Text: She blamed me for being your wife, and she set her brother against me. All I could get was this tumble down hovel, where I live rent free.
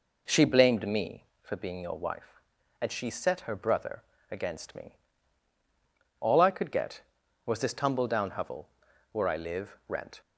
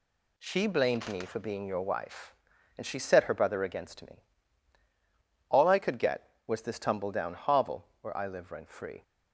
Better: second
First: pauses between "brother" and "against"; slight; at 4.0 s; 0.26 s long // stops before "free"; at 10.2 s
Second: none

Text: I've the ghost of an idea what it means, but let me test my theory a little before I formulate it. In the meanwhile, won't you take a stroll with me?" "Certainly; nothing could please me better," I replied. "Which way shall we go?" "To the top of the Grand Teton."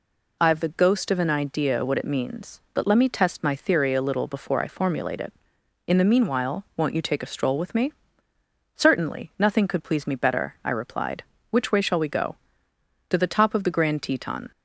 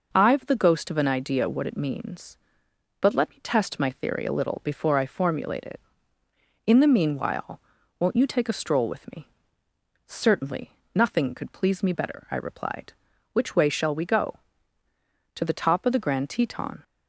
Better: neither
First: none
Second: none

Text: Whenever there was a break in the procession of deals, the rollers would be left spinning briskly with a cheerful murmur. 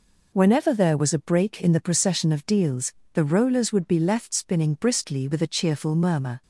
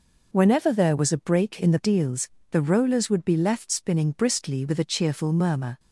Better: first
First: none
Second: skips "procession of"; at 1.8 s

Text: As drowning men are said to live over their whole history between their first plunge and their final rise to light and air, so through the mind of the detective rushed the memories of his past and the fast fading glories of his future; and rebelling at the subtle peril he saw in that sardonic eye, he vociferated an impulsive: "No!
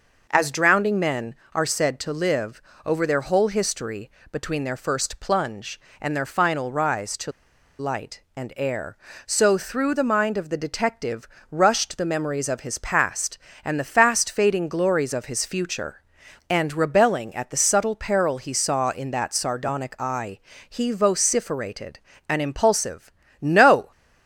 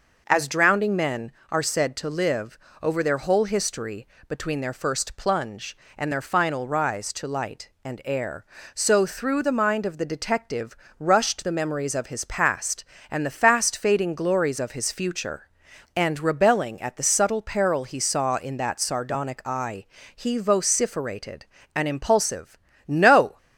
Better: second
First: pauses between "live" and "over"; slight; at 2.6 s; 0.24 s long // pauses between "history" and "between"; slight; at 4.0 s; 0.22 s long // pauses between "to" and "light"; noticeable; at 7.3 s; 0.47 s long // pauses between "detective" and "rushed"; slight; at 11.2 s; 0.20 s long // pauses between "vociferated" and "an"; slight; at 22.0 s; 0.26 s long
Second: pauses between "live" and "over"; slight; at 2.5 s; 0.24 s long // pauses between "history" and "between"; slight; at 4.0 s; 0.22 s long // pauses between "detective" and "rushed"; slight; at 10.7 s; 0.20 s long // pauses between "vociferated" and "an"; slight; at 21.4 s; 0.26 s long

